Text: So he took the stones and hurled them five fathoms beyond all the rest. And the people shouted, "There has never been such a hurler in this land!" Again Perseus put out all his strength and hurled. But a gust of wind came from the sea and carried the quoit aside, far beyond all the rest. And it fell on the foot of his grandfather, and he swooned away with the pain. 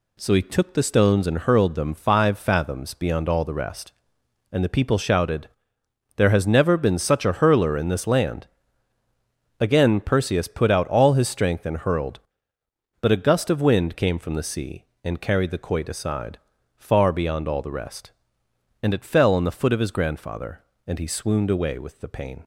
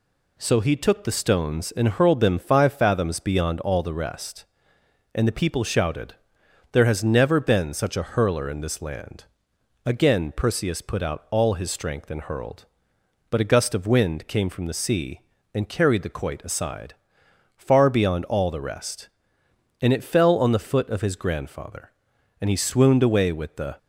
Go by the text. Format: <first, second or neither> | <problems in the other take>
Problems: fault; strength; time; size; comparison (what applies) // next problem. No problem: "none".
first | stops before "pain"; at 23.7 s